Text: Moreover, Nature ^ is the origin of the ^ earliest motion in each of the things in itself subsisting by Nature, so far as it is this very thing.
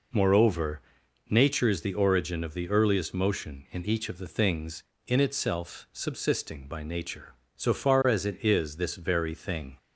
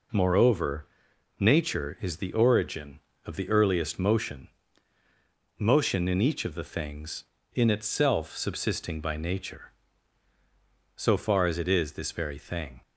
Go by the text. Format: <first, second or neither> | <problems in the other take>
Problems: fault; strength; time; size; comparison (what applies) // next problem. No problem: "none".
first | says "motion" twice; at 5.5 s